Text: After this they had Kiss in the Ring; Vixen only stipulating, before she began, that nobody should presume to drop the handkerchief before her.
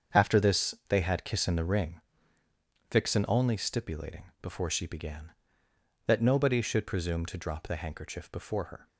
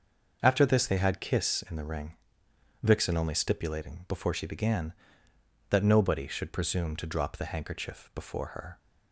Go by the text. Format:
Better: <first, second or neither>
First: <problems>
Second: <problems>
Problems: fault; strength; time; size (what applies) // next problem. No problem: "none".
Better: neither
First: starts louder than the rest; strong; until 1.2 s; 7.5 dB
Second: starts louder than the rest; until 1.4 s; 6 dB